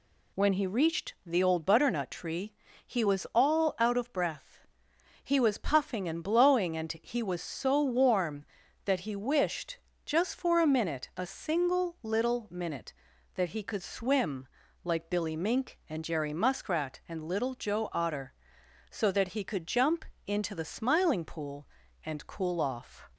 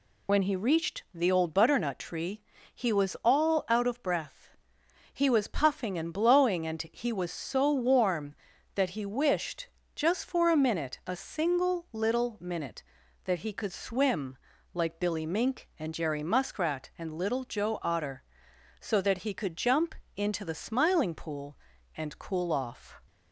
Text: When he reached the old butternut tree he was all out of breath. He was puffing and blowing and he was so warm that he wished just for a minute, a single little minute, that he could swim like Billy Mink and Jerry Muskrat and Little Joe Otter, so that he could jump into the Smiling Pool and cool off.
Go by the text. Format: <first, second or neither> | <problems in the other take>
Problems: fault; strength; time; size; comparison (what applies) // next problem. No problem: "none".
first | loses the start of "When"; at 0.2 s; 50 ms // pauses between "tree" and "he"; slight; at 2.4 s; 0.32 s long; slight in the first // pauses between "wished" and "just"; slight; at 9.6 s; 0.28 s long; slight in the first // pauses between "swim" and "like"; slight; at 14.3 s; 0.36 s long; slight in the first // pauses between "jump" and "into"; slight; at 19.9 s; 0.22 s long; slight in the first